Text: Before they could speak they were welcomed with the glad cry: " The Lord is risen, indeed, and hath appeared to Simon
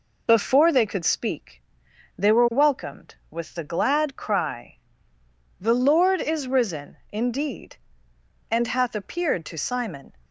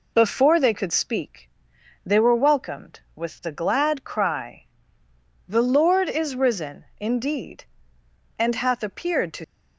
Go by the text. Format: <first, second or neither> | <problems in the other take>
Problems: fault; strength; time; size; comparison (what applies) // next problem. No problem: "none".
first | pauses between "speak" and "they"; noticeable; at 1.5 s; 0.52 s long; noticeable in the first // stops before "Simon"; at 9.4 s